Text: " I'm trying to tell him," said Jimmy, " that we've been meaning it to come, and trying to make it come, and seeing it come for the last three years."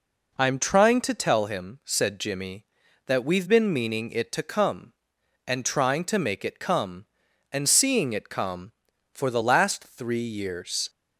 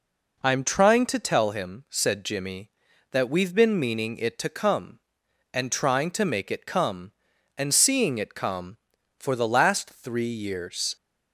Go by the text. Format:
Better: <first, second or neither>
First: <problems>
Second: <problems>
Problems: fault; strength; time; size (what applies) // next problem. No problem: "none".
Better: neither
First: none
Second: none